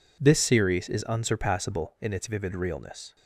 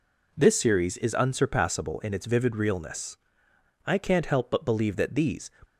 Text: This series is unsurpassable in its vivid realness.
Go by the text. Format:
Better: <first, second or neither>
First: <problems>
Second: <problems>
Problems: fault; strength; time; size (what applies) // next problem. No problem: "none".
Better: first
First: none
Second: goes on to say "I can't help but believe that these"; from 3.8 s on; 1.6 s long